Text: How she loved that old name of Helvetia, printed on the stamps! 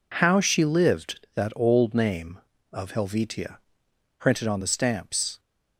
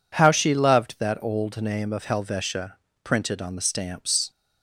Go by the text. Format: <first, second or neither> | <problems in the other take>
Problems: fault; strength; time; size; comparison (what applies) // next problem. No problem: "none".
second | says "lived" for "loved"; at 0.6 s